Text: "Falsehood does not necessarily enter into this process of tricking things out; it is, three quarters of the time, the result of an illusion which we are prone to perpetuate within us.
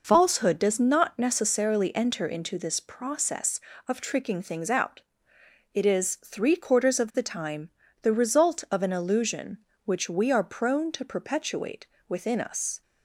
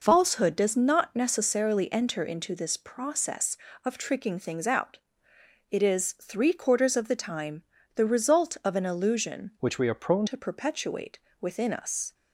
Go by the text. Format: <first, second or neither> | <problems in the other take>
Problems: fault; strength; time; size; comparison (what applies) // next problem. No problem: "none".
first | changes voice from "which" to "prone"; from 9.5 to 10.2 s; 0.7 s long // pauses between "perpetuate" and "within"; slight; at 11.1 s; 0.22 s long; slight in the first